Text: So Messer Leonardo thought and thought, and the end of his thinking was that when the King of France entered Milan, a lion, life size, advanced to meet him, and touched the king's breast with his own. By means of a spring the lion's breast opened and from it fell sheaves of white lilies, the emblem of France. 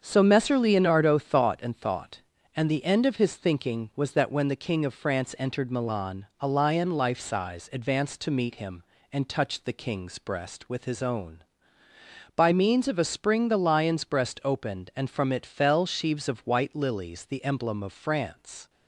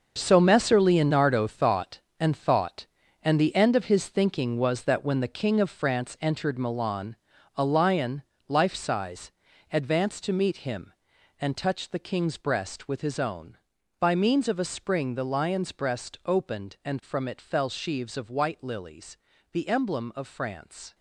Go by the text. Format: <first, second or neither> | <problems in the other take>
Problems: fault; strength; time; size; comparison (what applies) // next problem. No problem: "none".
first | gets quieter; strong; throughout; 10.5 dB // starts louder than the rest; noticeable; until 1.1 s; 6 dB; also in the first